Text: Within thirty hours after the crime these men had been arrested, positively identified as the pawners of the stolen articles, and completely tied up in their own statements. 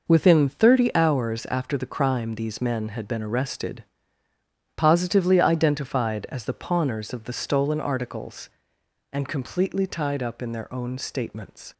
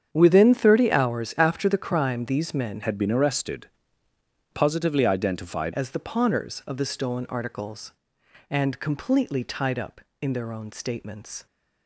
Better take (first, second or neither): first